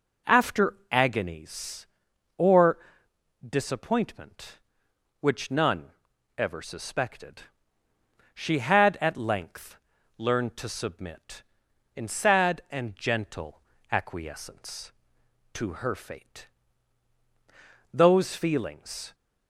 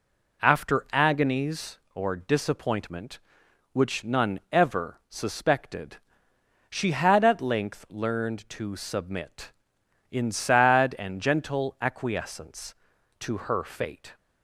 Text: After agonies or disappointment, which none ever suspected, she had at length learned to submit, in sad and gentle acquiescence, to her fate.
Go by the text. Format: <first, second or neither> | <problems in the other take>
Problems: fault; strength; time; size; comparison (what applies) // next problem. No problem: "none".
second | pauses between "After" and "agonies"; slight; at 0.7 s; 0.16 s long // pauses between "or" and "disappointment"; noticeable; at 2.7 s; 0.70 s long // pauses between "none" and "ever"; noticeable; at 5.8 s; 0.48 s long // pauses between "length" and "learned"; at 9.7 s; 0.40 s long // pauses between "gentle" and "acquiescence"; slight; at 13.6 s; 0.30 s long // goes on to say "Those feelings"; noticeable; from 17.9 s on; 1.2 s long